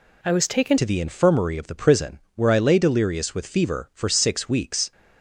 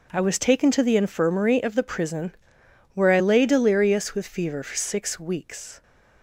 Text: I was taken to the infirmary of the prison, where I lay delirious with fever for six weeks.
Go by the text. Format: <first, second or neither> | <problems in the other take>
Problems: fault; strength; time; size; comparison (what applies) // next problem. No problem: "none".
second | changes voice at "to"; from 0.7 s on; 4.2 s long